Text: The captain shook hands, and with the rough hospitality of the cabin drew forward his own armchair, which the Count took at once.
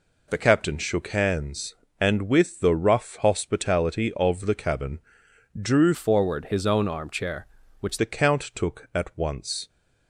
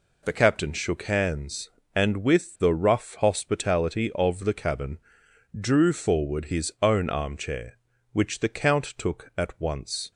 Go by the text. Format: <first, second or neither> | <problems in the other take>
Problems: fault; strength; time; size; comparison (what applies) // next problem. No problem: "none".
second | pauses between "cabin" and "drew"; noticeable; at 4.9 s; 0.60 s long; noticeable in the second // changes voice from "forward" to "which"; from 5.9 to 7.9 s; 2.0 s long